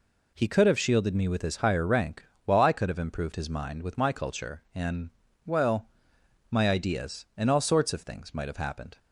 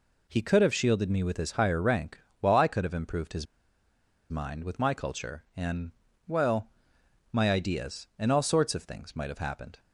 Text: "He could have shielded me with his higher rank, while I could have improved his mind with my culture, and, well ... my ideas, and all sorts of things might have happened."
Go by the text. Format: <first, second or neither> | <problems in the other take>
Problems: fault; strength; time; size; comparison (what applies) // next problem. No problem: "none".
first | pauses between "his" and "mind"; noticeable; at 3.4 s; 0.86 s long